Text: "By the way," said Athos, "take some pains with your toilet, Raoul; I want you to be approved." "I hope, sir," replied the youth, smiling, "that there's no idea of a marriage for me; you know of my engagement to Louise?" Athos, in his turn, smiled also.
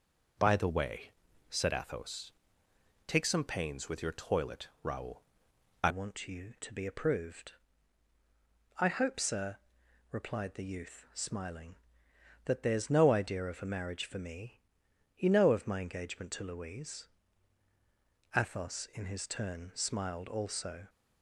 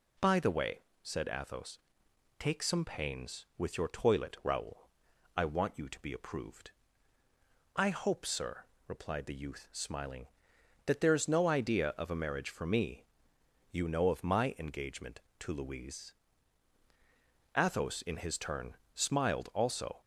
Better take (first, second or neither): second